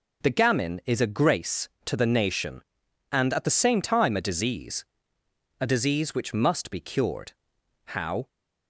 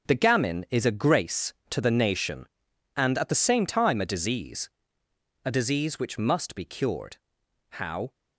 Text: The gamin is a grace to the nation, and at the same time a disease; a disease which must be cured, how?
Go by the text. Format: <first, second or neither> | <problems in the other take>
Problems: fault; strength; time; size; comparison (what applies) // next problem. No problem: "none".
first | gets quieter; strong; throughout; 9.5 dB